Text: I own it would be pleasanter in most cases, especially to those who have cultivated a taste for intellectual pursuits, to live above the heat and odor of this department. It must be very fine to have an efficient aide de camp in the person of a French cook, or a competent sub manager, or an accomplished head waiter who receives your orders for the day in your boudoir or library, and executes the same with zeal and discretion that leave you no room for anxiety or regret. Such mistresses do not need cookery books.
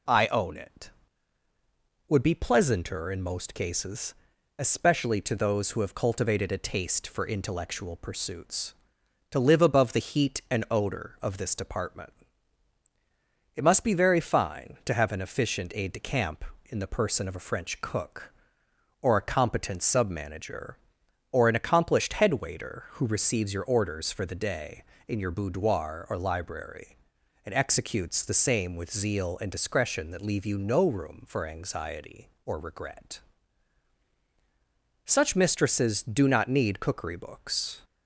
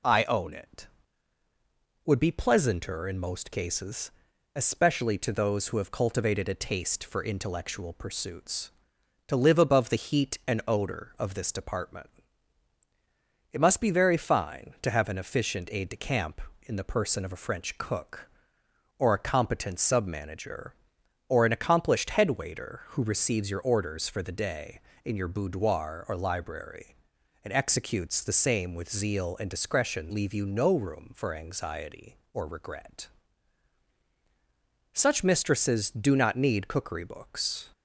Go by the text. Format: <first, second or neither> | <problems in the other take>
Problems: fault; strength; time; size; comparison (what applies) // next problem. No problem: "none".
first | skips "that"; at 30.1 s